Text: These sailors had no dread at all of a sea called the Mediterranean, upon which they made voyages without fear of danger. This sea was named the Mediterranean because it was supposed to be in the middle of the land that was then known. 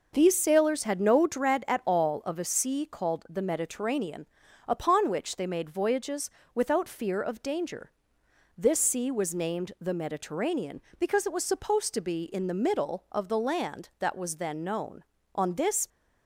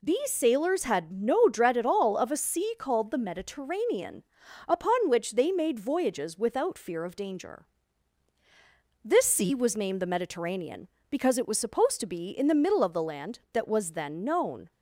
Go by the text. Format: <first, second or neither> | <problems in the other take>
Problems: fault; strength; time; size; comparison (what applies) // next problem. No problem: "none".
second | pauses between "voyages" and "without"; slight; at 6.3 s; 0.24 s long // goes on to say "On this"; from 15.3 s on; 0.54 s long